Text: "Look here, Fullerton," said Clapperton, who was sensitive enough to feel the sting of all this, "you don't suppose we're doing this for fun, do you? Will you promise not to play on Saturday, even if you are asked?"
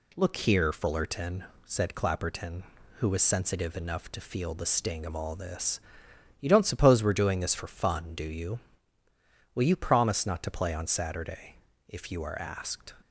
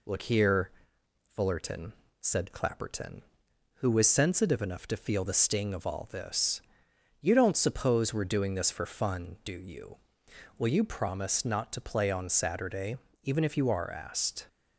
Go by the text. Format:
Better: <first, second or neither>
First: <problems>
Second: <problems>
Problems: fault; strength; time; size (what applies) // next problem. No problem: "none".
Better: second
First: skips "even"; at 11.7 s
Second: none